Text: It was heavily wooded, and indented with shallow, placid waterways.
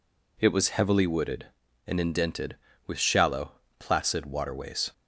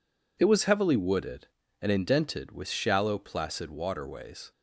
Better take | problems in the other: neither | none

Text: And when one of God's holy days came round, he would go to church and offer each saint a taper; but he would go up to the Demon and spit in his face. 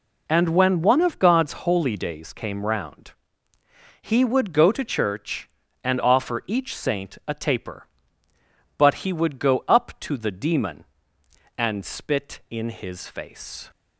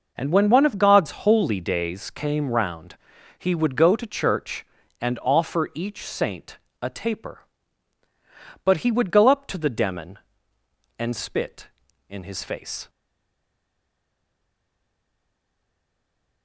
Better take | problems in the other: first | pauses between "saint" and "a"; slight; at 6.5 s; 0.24 s long // stays silent after the last word; strong; from 12.8 s on; 3.6 s long

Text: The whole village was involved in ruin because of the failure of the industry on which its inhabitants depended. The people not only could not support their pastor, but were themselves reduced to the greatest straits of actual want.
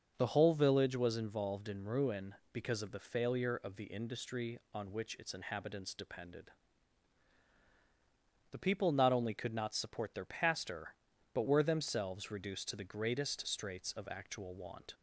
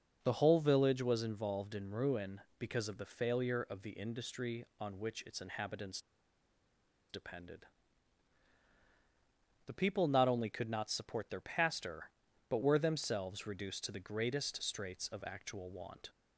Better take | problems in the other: first | pauses between "inhabitants" and "depended"; at 5.9 s; 1.1 s long

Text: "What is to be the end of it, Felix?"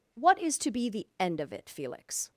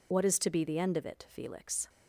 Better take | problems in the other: first | loses the start of "What"; at 0.1 s; 40 ms

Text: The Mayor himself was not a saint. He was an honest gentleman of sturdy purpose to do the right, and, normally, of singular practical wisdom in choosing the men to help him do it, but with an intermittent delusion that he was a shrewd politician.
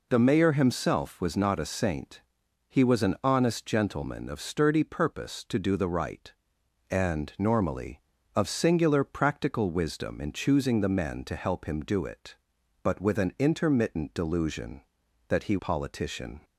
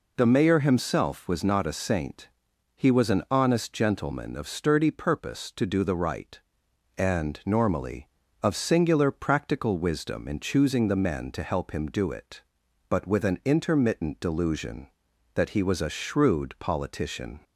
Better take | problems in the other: second | skips "was a shrewd"; at 15.5 s

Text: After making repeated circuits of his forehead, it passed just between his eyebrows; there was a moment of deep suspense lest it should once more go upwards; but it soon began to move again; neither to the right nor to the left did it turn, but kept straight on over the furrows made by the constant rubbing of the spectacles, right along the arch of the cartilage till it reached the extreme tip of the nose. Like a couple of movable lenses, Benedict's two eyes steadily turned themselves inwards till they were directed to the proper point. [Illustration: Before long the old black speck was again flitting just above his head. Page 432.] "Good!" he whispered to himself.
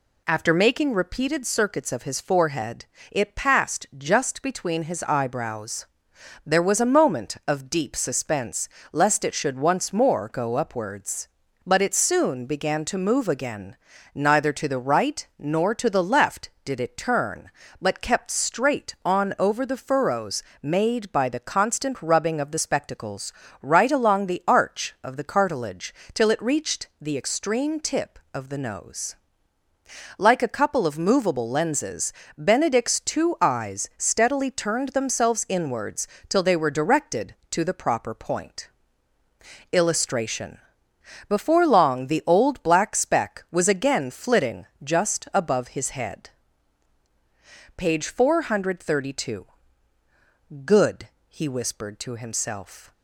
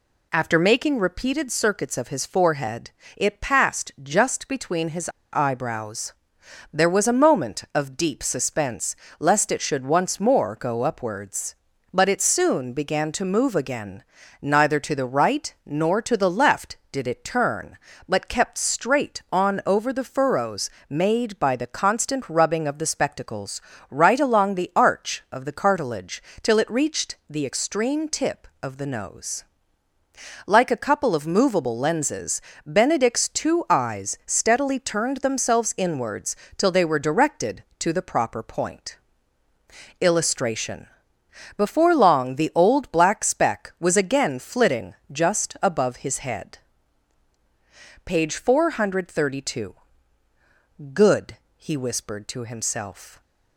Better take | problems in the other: first | pauses between "his" and "eyebrows"; slight; at 5.0 s; 0.23 s long // pauses between "suspense" and "lest"; slight; at 8.9 s; 0.24 s long; slight in the first // pauses between "furrows" and "made"; slight; at 20.6 s; 0.20 s long; slight in the first // pauses between "cartilage" and "till"; slight; at 26.2 s; 0.22 s long; slight in the first // pauses between "inwards" and "till"; slight; at 36.3 s; 0.22 s long; slight in the first // pauses between "flitting" and "just"; slight; at 44.9 s; 0.18 s long; slight in the first

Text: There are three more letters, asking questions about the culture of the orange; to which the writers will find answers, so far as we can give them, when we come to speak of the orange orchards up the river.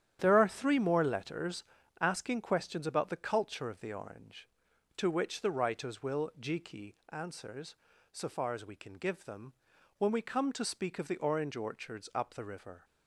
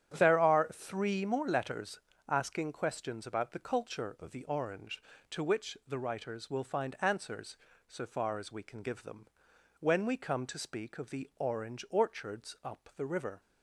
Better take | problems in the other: second | starts louder than the rest; strong; until 1.2 s; 10 dB; strong in the second // says "jiki" for "find"; at 6.3 s

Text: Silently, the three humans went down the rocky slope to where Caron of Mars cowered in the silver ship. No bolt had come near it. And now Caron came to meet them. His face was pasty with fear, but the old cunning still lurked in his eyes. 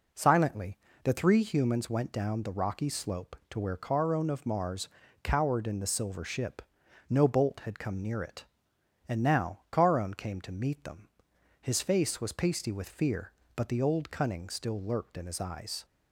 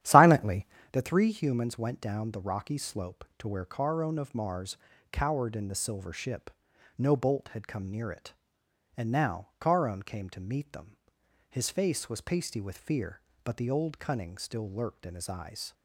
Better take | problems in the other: first | starts louder than the rest; strong; until 0.9 s; 11.5 dB // pauses between "Mars" and "cowered"; slight; at 4.7 s; 0.34 s long; slight in the first

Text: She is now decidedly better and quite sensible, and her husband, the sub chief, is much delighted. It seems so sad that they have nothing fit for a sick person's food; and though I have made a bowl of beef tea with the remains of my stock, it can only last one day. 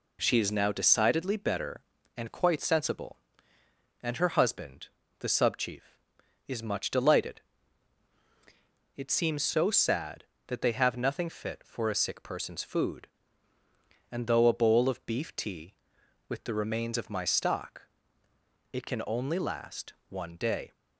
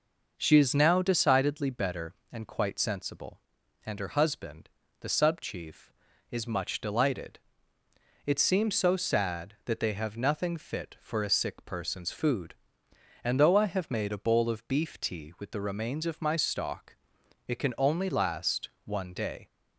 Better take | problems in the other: second | skips "I have made"; at 14.4 s // pauses between "last" and "one"; slight; at 19.9 s; 0.16 s long; slight in the second

